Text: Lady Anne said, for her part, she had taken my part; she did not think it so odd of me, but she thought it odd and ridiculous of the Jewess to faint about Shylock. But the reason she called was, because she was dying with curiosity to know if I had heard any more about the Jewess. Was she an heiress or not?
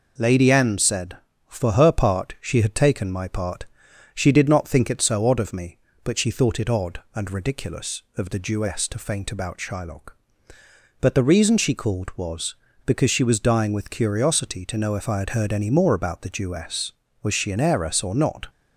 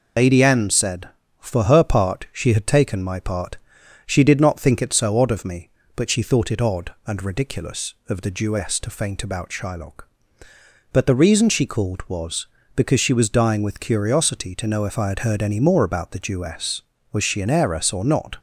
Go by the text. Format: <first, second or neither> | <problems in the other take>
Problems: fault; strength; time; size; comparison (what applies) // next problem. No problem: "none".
first | loses the start of "Lady"; at 0.1 s; 75 ms